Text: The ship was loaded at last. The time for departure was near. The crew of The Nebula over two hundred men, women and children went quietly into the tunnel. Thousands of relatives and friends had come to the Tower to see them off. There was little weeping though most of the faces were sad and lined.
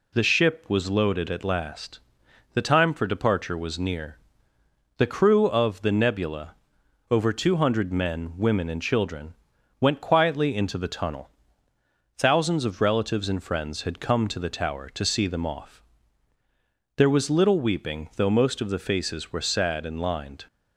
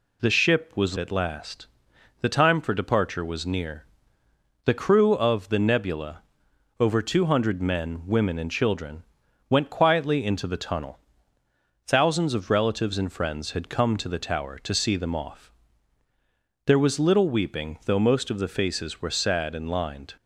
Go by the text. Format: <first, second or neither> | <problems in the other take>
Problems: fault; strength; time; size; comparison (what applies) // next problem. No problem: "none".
first | skips "loaded"; at 0.9 s // pauses between "Nebula" and "over"; noticeable; at 6.2 s; 0.58 s long; noticeable in the first // pauses between "children" and "went"; noticeable; at 9.0 s; 0.46 s long; noticeable in the first